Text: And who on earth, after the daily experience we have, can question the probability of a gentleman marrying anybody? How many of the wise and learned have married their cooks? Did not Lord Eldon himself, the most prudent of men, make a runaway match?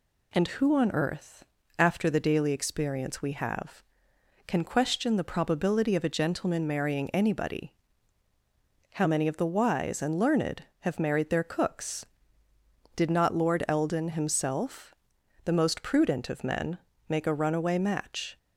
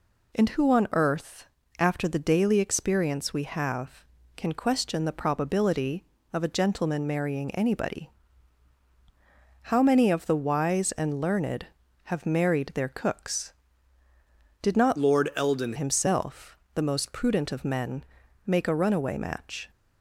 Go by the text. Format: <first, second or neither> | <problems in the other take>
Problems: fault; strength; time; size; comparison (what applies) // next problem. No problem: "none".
first | changes voice from "Lord" to "Eldon"; from 14.9 to 15.7 s; 0.8 s long